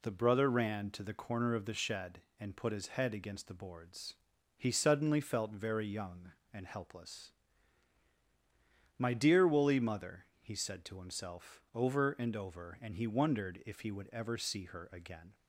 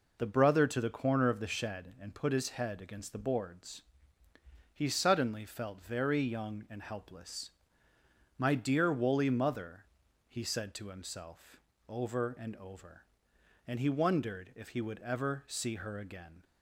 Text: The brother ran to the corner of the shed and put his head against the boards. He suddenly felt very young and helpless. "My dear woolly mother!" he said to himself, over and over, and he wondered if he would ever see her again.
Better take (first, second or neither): first